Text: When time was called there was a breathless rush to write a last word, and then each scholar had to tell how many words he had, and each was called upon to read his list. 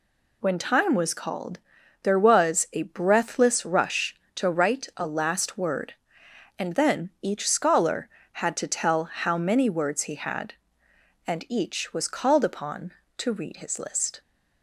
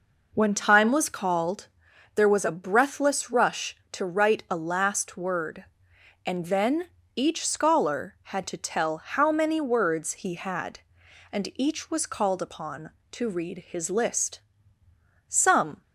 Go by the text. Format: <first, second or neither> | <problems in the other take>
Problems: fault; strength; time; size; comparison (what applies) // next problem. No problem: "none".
first | pauses between "called" and "there"; noticeable; at 1.6 s; 0.48 s long; also in the first // pauses between "then" and "each"; slight; at 6.8 s; 0.26 s long // goes on to say "Some"; from 15.2 s on; 0.54 s long